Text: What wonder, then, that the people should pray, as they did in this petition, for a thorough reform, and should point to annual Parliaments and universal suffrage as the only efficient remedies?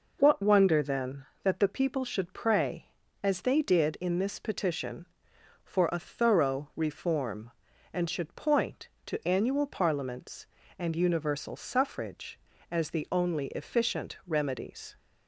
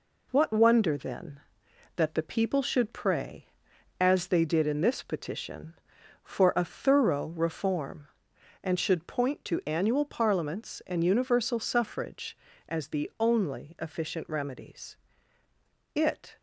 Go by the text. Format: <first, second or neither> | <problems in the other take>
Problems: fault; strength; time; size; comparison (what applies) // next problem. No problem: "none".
first | goes on to say "It"; slight; from 15.9 s on; 0.42 s long